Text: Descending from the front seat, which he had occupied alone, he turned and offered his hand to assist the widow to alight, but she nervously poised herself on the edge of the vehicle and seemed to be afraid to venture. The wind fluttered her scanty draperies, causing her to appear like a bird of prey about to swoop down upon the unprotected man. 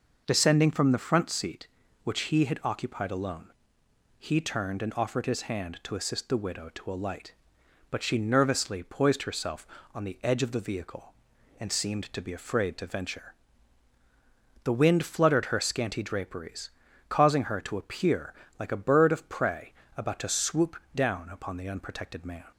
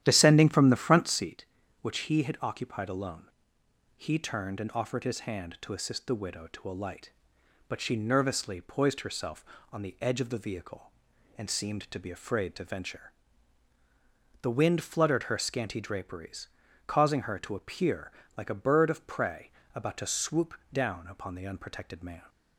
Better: first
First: pauses between "appear" and "like"; slight; at 18.3 s; 0.24 s long // pauses between "prey" and "about"; slight; at 19.7 s; 0.22 s long // pauses between "swoop" and "down"; slight; at 20.7 s; 0.20 s long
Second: starts louder than the rest; strong; until 1.3 s; 11 dB // pauses between "appear" and "like"; slight; at 18.1 s; 0.24 s long // pauses between "prey" and "about"; slight; at 19.5 s; 0.22 s long // pauses between "swoop" and "down"; slight; at 20.5 s; 0.20 s long

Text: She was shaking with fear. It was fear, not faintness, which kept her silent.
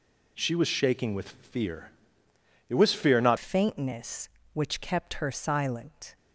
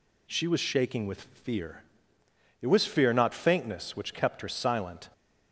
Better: second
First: changes voice at "faintness"; from 3.3 s on; 2.8 s long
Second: none

